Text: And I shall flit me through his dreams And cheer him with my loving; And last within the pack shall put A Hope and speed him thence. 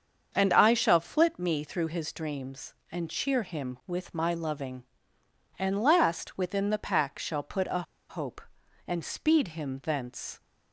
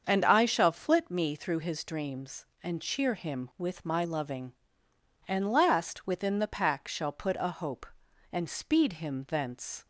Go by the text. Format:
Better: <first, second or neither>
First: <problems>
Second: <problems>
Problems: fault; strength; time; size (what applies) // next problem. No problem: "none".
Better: second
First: starts louder than the rest; until 1.3 s; 7 dB // pauses between "A" and "Hope"; slight; at 7.8 s; 0.27 s long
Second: starts louder than the rest; until 1.0 s; 7 dB